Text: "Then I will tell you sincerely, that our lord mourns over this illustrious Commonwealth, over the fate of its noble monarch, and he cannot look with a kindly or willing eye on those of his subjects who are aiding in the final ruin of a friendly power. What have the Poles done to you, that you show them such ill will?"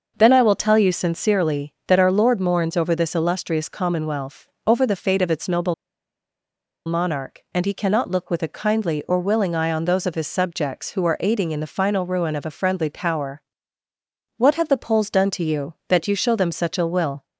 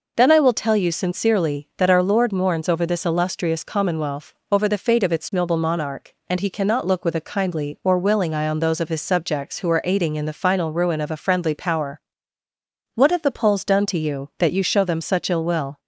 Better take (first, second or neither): second